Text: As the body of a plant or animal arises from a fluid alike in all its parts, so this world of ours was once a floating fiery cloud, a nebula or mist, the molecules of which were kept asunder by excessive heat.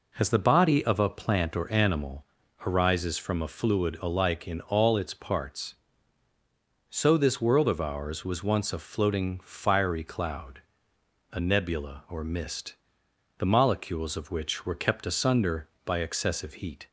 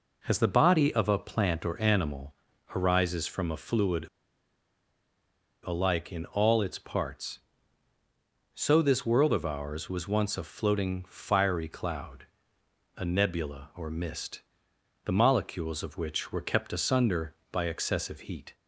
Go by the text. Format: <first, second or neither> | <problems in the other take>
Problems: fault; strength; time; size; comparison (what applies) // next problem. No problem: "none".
first | pauses between "animal" and "arises"; at 2.3 s; 0.44 s long; also in the first // pauses between "fluid" and "alike"; strong; at 4.0 s; 1.6 s long